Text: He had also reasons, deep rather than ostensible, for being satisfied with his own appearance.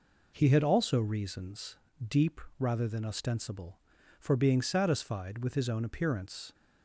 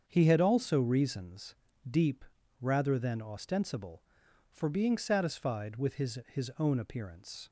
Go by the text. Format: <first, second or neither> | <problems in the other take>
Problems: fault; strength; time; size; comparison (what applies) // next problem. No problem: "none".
first | starts louder than the rest; until 1.0 s; 7 dB // pauses between "deep" and "rather"; slight; at 2.2 s; 0.36 s long; slight in the first // says "his" twice; at 6.2 s